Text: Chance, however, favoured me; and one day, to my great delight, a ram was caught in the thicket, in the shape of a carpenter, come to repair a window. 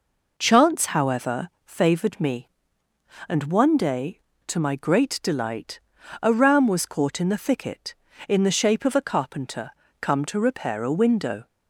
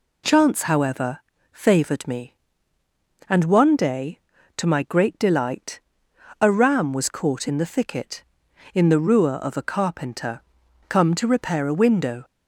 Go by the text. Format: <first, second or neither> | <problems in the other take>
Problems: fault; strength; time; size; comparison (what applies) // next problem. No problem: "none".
first | says "ruer" for "shape"; at 8.9 s